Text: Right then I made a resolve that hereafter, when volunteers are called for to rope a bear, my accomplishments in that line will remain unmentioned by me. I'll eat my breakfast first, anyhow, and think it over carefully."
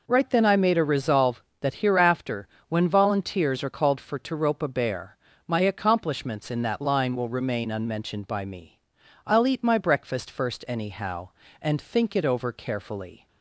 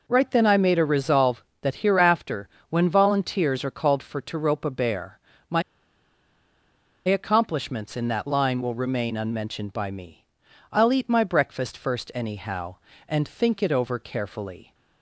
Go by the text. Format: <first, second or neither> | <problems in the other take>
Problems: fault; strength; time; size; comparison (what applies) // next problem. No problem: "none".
first | pauses between "my" and "accomplishments"; strong; at 5.6 s; 1.4 s long